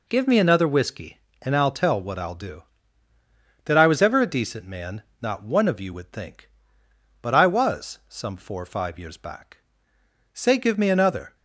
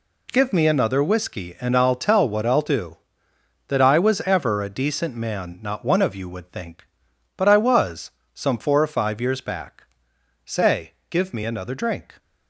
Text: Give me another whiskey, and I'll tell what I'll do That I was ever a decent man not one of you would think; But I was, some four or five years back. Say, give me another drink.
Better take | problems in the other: second | pauses between "man" and "not"; slight; at 5.0 s; 0.18 s long // stops before "drink"; at 11.3 s

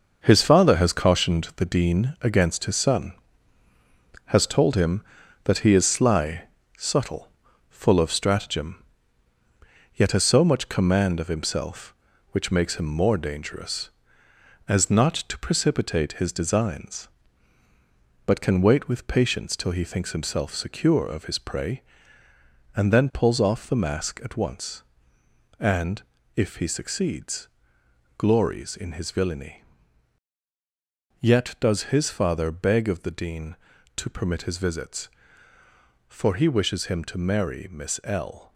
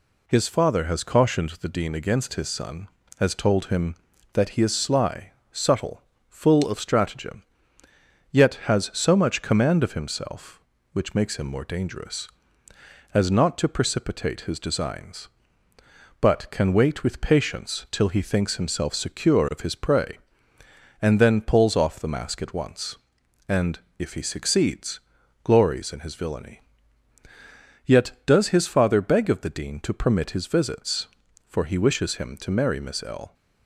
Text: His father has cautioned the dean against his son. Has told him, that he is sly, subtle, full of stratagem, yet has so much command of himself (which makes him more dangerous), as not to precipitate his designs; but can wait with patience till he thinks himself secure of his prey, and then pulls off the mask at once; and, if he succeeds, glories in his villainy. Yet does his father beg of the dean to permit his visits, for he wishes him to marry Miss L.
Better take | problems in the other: second | gets quieter; strong; throughout; 7.5 dB

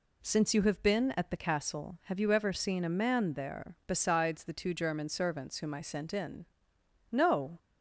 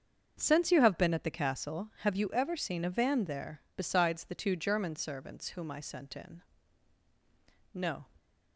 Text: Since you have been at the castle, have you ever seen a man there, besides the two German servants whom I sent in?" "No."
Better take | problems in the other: first | starts louder than the rest; until 1.4 s; 6.5 dB // says "van" for "man"; at 2.9 s

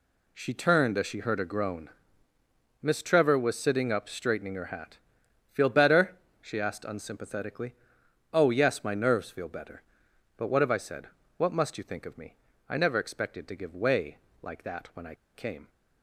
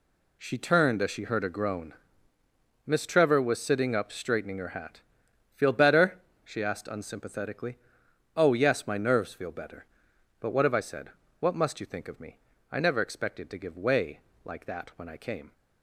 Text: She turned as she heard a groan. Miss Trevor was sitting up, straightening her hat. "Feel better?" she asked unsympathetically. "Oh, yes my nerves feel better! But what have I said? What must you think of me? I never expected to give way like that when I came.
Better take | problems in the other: second | pauses between "way" and "like"; slight; at 14.1 s; 0.26 s long; slight in the second // pauses between "I" and "came"; slight; at 15.1 s; 0.20 s long

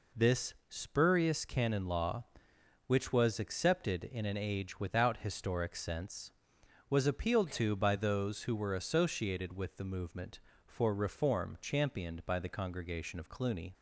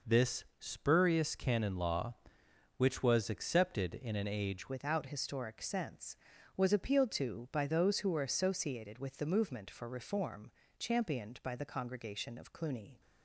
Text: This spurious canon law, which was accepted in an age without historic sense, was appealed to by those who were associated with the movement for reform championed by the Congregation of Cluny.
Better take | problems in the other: first | pauses between "This" and "spurious"; slight; at 0.4 s; 0.16 s long; slight in the first // changes voice at "without"; from 4.6 s on; 8.4 s long // pauses between "reform" and "championed"; slight; at 10.5 s; 0.26 s long

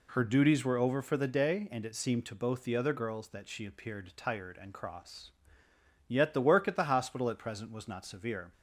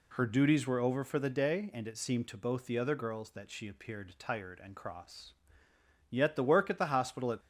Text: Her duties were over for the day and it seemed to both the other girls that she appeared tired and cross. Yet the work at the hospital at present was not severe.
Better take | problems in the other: first | stops before "present was not severe"; at 7.3 s

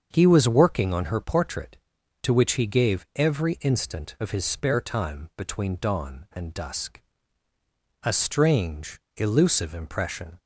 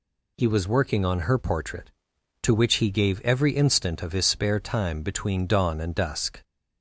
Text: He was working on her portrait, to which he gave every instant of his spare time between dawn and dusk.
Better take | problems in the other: second | starts louder than the rest; until 1.1 s; 7 dB // goes on to say "A strange elusive impression"; strong; from 8.0 s on; 2.3 s long

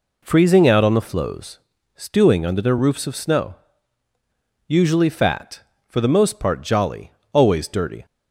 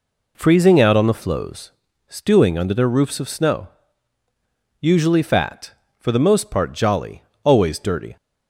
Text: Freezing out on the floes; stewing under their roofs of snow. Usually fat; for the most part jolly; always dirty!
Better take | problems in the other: neither | none

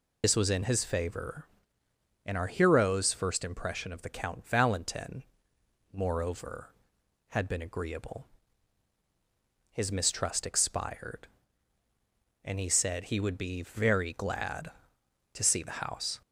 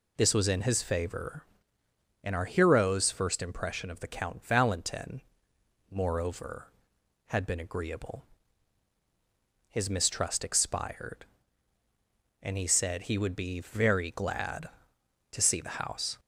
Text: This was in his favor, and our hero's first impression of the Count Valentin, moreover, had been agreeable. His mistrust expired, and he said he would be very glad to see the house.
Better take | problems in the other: second | loses the start of "This"; at 0.2 s; 45 ms

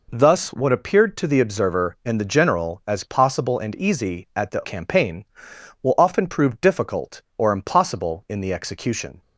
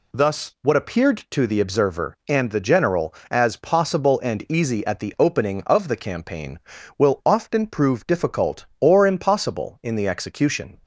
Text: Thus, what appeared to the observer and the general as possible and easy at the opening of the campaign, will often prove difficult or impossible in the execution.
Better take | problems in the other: second | skips "opening of the"; at 4.6 s

